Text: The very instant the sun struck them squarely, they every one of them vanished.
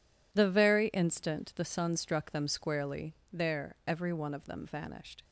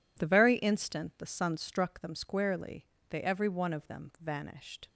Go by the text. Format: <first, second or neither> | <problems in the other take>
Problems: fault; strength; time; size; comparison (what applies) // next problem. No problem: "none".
second | says "there" for "they"; at 3.3 s